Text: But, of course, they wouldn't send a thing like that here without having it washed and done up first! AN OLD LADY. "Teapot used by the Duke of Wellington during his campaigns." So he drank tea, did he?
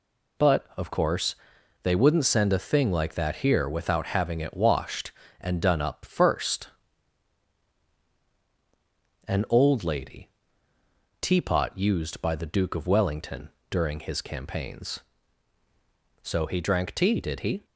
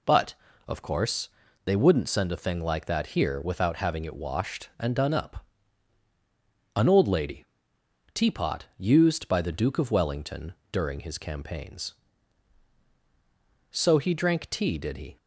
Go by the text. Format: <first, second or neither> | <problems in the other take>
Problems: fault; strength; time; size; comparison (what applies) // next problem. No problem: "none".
first | skips "first"; at 6.1 s // pauses between "Wellington" and "during"; slight; at 10.5 s; 0.18 s long; slight in the first